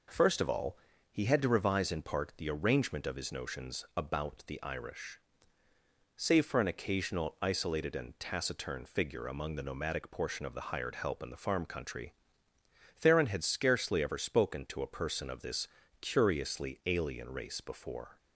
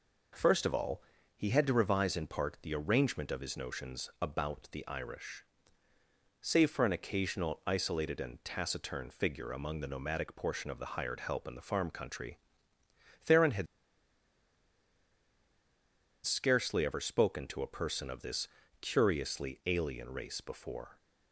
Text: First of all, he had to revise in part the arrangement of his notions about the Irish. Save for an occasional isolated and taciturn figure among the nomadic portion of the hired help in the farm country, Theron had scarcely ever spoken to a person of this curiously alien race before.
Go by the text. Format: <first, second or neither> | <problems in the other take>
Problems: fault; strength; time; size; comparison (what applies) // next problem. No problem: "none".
first | pauses between "had" and "scarcely"; strong; at 13.6 s; 2.5 s long // pauses between "this" and "curiously"; slight; at 18.4 s; 0.34 s long; slight in the first